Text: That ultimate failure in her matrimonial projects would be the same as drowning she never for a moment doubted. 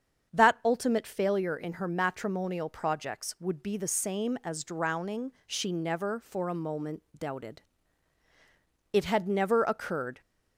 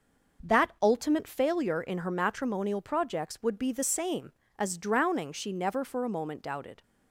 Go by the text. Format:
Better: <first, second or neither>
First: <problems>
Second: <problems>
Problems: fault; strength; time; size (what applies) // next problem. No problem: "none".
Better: second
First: starts louder than the rest; strong; until 1.3 s; 7.5 dB // pauses between "drowning" and "she"; slight; at 5.3 s; 0.16 s long // goes on to say "It had never occurred"; noticeable; from 8.9 s on; 1.2 s long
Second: starts louder than the rest; noticeable; until 1.5 s; 6 dB